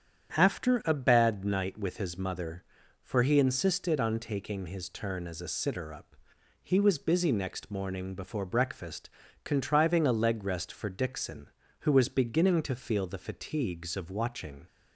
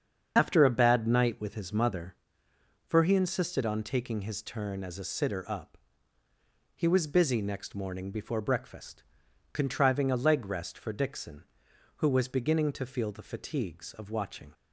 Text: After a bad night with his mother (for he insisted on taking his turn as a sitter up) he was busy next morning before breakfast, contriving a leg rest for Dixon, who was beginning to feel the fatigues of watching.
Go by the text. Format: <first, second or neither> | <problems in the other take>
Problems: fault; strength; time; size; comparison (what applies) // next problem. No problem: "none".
first | loses the start of "After"; at 0.3 s; 70 ms // starts louder than the rest; strong; until 1.3 s; 7 dB; strong in the first